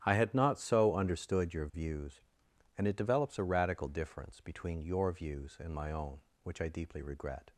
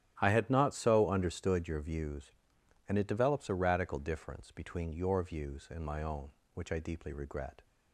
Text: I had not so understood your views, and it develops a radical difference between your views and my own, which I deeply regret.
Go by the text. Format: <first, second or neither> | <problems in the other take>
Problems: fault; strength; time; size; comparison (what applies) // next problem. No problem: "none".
neither | starts louder than the rest; strong; the same in both